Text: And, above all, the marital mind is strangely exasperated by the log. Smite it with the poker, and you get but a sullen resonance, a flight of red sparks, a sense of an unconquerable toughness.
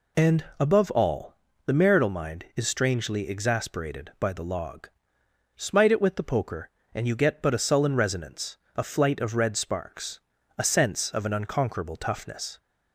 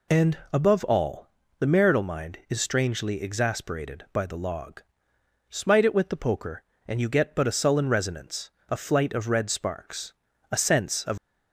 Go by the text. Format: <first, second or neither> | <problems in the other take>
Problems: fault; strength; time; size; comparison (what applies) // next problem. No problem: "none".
first | stops before "an unconquerable toughness"; at 11.1 s